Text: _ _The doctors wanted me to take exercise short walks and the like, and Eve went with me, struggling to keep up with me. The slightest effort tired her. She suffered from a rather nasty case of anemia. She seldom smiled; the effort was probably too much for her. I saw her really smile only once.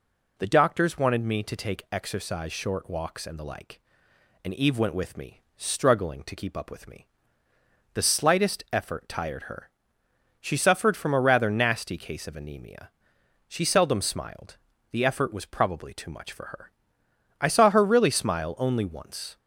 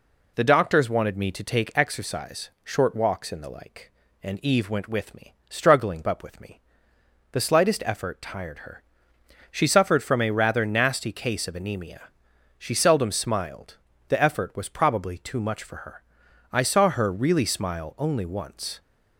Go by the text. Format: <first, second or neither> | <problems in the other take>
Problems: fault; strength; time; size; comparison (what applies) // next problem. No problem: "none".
first | skips "to keep"; at 6.0 s